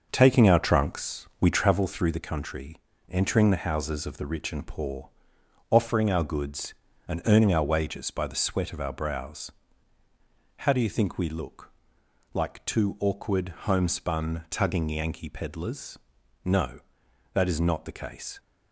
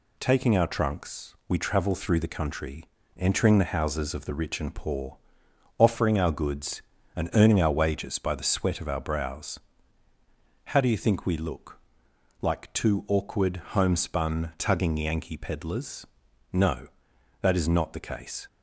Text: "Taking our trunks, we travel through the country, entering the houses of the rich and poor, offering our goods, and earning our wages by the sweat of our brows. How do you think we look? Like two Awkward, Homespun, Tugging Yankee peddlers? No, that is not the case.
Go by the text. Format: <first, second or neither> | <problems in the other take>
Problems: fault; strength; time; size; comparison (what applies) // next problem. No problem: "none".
second | starts louder than the rest; until 1.9 s; 6 dB